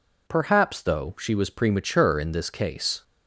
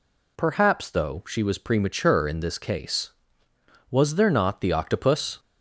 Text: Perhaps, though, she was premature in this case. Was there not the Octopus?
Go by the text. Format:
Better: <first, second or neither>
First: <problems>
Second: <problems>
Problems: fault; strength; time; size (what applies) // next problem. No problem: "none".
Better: second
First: stops before "Was there not the Octopus"; at 3.0 s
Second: none